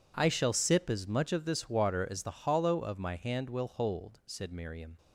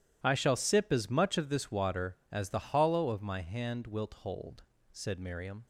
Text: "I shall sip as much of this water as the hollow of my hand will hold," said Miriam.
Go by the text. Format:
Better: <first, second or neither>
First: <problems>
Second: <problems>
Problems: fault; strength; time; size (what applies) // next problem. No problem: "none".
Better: first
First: none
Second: starts louder than the rest; strong; until 1.2 s; 12.5 dB // says "wilt" for "will"; at 3.8 s